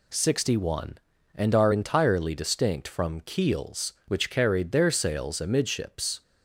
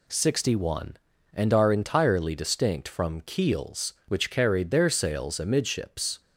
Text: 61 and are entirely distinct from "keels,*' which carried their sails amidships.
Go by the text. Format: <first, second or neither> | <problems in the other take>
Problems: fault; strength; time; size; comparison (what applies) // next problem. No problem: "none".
neither | none